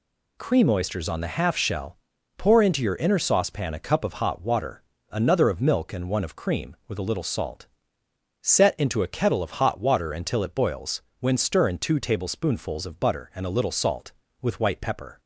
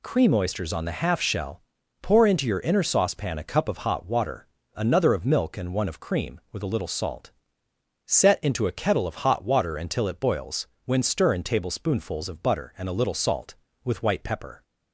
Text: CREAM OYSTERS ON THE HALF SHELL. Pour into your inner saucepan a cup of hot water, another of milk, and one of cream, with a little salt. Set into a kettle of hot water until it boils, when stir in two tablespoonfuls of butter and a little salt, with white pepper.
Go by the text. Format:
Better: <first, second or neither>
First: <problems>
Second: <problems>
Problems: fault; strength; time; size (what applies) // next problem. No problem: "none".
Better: first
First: none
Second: skips "two"; at 11.4 s